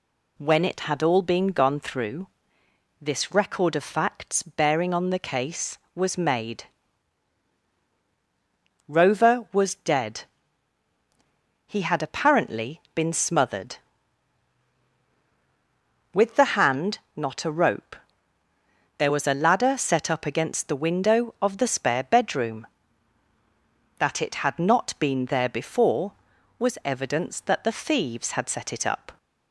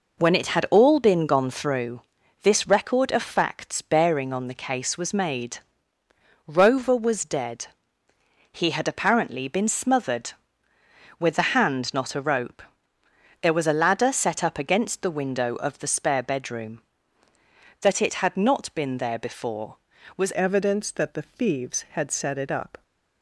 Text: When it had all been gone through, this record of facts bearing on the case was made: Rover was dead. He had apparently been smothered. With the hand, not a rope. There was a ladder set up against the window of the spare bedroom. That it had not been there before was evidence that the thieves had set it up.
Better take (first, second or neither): first